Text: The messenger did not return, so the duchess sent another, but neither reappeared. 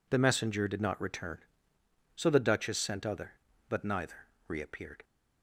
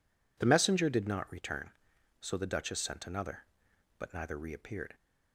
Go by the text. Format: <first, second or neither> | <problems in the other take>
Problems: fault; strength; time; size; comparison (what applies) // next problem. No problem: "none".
second | says "other" for "another"; at 3.0 s // pauses between "neither" and "reappeared"; slight; at 4.2 s; 0.20 s long